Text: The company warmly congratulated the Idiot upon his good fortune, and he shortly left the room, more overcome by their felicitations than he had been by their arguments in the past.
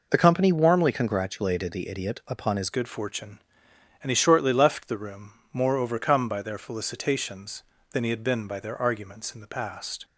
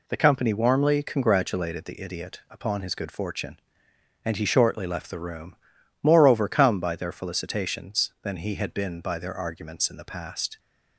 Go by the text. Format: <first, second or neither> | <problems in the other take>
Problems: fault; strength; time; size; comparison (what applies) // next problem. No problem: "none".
second | changes voice at "good"; from 2.7 s on; 7.3 s long